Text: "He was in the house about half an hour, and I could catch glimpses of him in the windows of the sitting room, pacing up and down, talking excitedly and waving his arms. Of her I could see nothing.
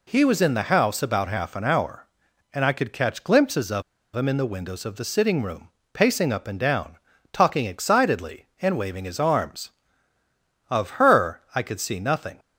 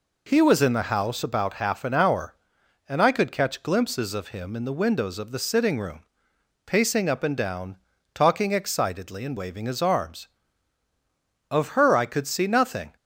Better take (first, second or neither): second